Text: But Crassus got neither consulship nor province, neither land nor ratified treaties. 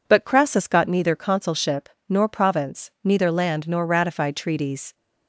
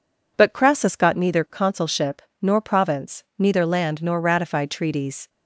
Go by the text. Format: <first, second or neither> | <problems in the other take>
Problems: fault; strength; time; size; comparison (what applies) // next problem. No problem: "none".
neither | pauses between "consulship" and "nor"; slight; the same in both